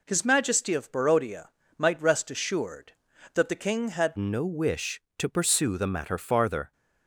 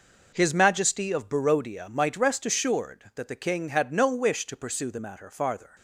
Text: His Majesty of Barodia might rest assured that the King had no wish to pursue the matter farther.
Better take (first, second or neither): second